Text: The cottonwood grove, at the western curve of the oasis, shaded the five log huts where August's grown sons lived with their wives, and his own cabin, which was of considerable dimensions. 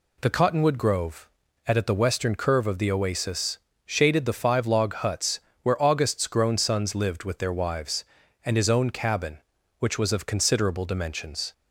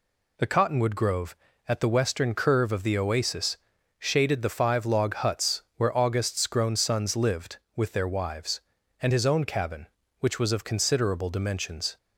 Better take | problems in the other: second | says "at" twice; at 1.7 s // pauses between "huts" and "where"; slight; at 5.3 s; 0.24 s long

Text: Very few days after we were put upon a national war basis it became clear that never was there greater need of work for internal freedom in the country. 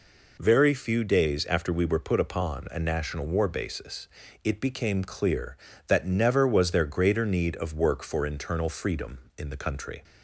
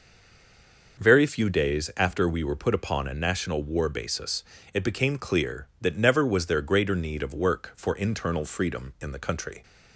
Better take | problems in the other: first | stays silent before the first word; until 0.9 s; 0.9 s long // pauses between "basis" and "it"; slight; at 4.4 s; 0.32 s long; slight in the first

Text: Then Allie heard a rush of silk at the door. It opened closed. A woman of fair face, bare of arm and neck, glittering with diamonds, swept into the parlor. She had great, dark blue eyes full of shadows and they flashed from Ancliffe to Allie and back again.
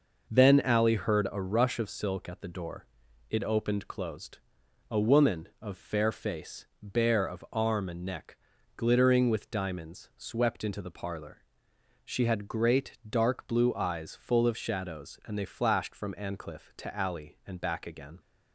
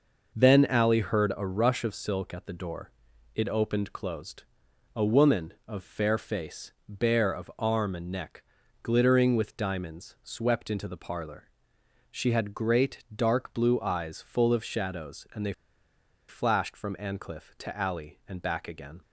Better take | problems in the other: first | pauses between "they" and "flashed"; noticeable; at 15.5 s; 0.75 s long

